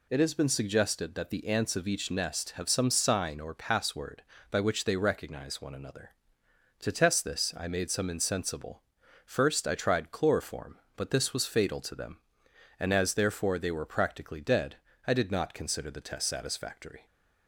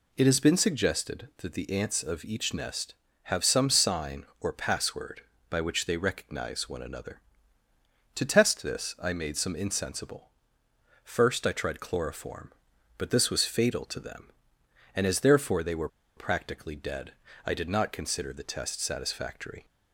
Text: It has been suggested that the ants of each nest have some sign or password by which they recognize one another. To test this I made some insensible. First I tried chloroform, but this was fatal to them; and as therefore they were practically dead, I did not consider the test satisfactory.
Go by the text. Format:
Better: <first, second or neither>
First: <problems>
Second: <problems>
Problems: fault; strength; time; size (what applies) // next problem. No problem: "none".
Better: first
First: none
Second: pauses between "were" and "practically"; slight; at 15.8 s; 0.28 s long